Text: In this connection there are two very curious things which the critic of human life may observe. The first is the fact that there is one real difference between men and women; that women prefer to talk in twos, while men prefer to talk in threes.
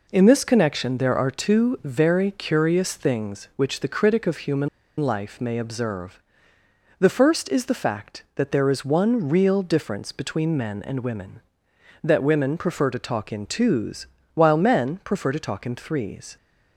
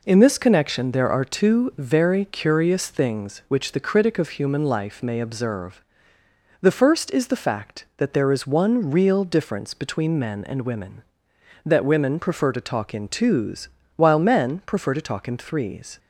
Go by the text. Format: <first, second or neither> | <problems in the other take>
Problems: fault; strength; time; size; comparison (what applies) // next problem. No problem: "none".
second | pauses between "human" and "life"; slight; at 4.6 s; 0.31 s long